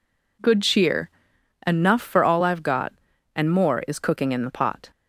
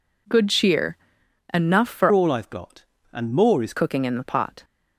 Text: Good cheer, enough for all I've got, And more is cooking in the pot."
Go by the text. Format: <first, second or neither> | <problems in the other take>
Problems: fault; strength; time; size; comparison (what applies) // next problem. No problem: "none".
first | changes voice from "all" to "is"; from 2.1 to 3.7 s; 1.6 s long